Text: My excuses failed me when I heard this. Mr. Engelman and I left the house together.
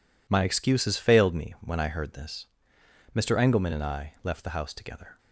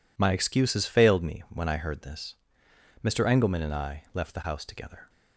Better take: neither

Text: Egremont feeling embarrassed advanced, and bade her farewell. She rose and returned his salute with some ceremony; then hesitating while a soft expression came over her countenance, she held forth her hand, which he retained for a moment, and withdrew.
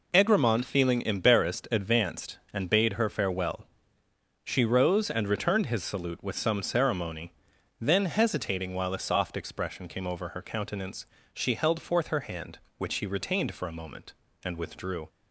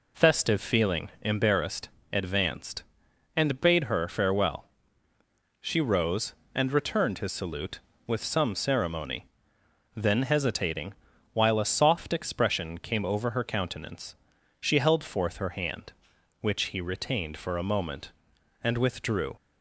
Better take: first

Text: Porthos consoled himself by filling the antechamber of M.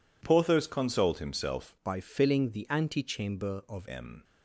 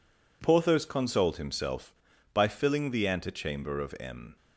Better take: second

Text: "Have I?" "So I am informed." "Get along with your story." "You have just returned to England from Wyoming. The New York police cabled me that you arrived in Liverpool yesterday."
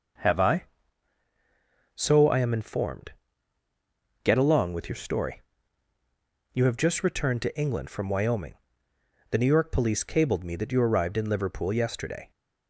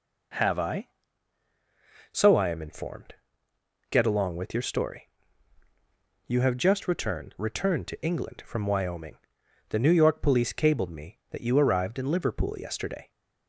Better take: first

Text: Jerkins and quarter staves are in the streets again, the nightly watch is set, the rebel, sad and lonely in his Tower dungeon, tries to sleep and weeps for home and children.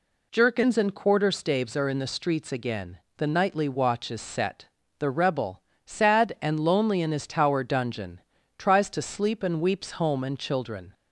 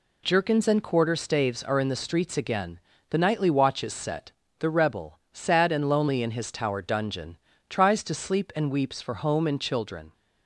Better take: second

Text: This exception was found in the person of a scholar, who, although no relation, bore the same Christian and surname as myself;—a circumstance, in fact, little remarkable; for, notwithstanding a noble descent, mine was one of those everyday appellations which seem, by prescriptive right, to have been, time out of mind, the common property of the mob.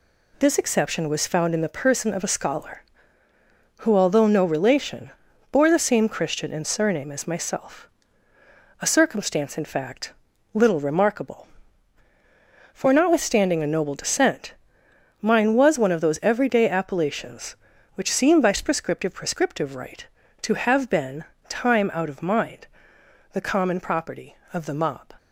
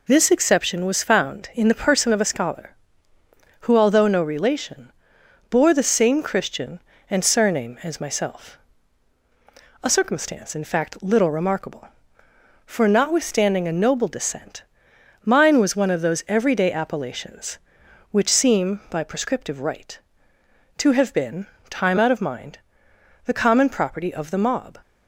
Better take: second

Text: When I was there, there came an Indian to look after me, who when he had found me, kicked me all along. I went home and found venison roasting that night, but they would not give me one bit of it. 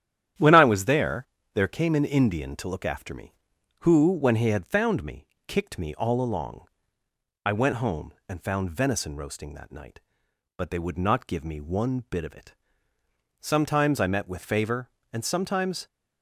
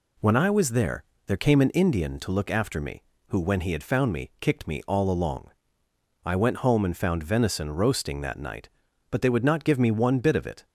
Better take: second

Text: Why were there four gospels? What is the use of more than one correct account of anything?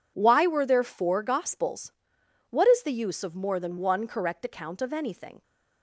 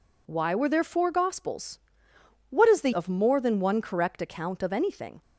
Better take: first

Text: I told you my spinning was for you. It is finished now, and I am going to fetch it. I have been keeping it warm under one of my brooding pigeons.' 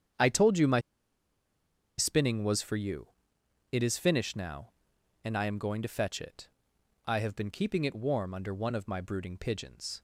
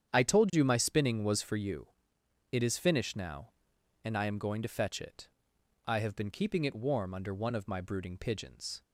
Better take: second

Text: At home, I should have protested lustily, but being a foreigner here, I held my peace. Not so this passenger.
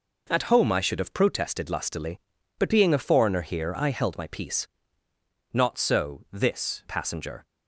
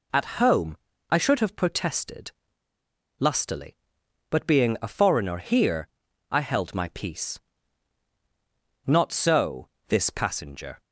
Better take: first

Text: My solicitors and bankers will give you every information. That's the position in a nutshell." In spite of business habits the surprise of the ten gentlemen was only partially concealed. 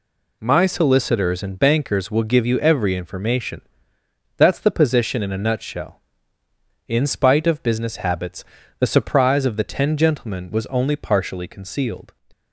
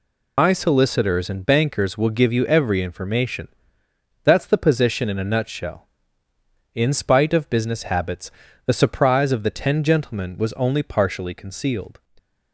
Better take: first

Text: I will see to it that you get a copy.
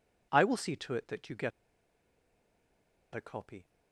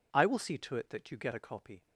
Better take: second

